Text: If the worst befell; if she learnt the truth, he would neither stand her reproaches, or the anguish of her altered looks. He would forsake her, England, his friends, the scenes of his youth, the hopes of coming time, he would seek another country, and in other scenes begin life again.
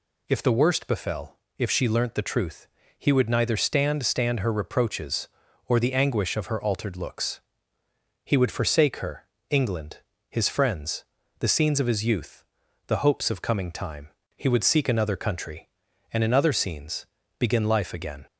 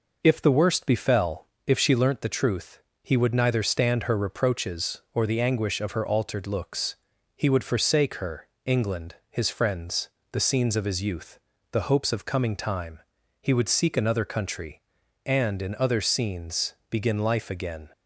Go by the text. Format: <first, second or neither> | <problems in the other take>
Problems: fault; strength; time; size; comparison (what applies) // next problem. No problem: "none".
second | says "stand" twice; at 4.0 s // pauses between "scenes" and "begin"; slight; at 17.0 s; 0.32 s long; slight in the second